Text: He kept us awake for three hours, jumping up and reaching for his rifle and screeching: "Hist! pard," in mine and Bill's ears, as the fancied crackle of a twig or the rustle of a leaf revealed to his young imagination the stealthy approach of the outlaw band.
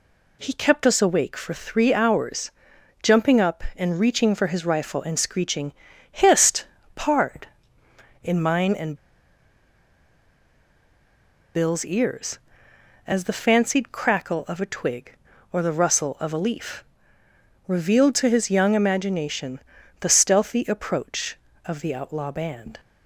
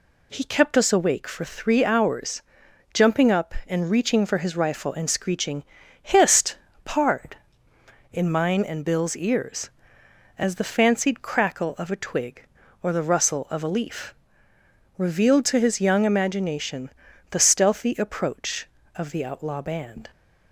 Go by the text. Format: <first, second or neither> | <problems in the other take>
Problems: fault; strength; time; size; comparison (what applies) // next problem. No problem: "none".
second | pauses between "and" and "Bill's"; strong; at 8.9 s; 2.5 s long // pauses between "leaf" and "revealed"; noticeable; at 16.8 s; 0.84 s long; noticeable in the second // pauses between "imagination" and "the"; at 19.5 s; 0.40 s long; also in the second